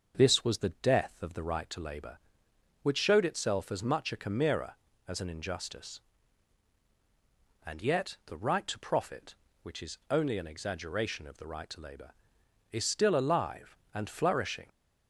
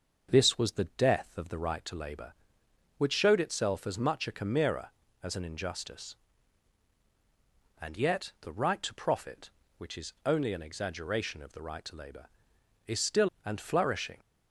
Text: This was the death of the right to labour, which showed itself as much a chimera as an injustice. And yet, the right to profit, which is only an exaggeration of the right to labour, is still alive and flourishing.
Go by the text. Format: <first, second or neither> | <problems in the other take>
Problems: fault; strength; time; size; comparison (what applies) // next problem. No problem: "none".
first | starts louder than the rest; until 1.3 s; 6.5 dB; also in the first // skips "alive"; at 13.3 s